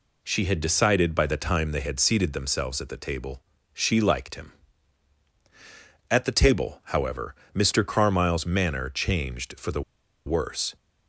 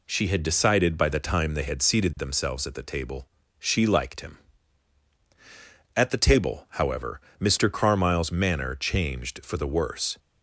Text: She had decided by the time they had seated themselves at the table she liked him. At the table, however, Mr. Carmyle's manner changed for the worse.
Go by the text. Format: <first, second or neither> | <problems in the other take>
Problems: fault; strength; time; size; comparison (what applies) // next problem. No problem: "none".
second | pauses between "table" and "she"; slight; at 3.4 s; 0.34 s long; slight in the second // pauses between "the" and "worse"; at 9.8 s; 0.45 s long